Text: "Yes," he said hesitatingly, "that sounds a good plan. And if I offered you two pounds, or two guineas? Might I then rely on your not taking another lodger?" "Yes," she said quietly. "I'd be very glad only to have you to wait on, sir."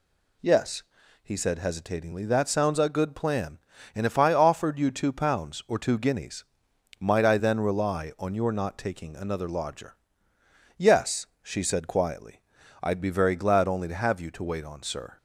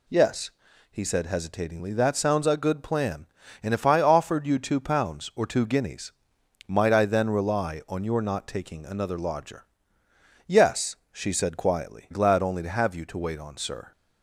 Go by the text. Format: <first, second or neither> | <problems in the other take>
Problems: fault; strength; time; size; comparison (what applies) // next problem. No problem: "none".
first | skips "I'd be very"; at 12.1 s